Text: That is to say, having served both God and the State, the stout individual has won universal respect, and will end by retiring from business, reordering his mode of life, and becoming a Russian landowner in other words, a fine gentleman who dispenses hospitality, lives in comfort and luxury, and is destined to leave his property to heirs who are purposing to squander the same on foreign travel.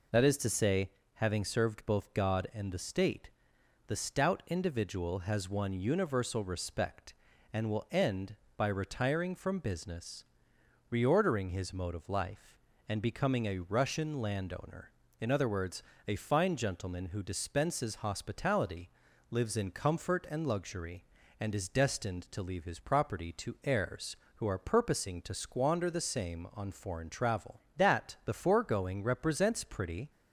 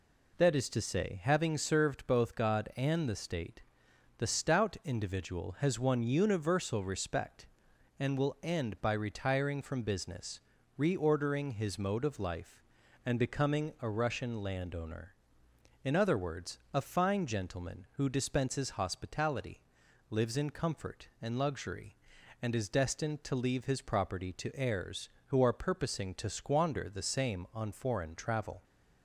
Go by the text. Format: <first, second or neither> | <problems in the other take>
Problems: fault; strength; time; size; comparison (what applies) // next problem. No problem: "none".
second | goes on to say "That the foregoing represents pretty"; strong; from 27.7 s on; 2.3 s long